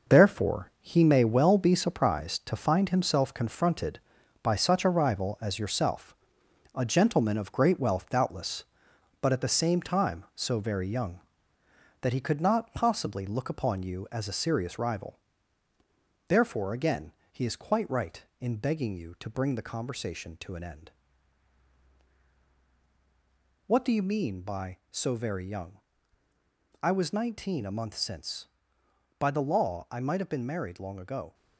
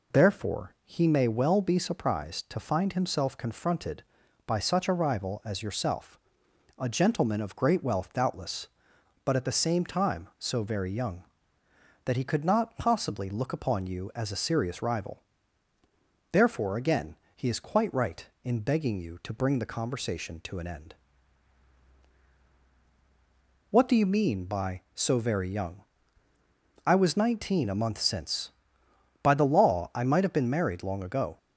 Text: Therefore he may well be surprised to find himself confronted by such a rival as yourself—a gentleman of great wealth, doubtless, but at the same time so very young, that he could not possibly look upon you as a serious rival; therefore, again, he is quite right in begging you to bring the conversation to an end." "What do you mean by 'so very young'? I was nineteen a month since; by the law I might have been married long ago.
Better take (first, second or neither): second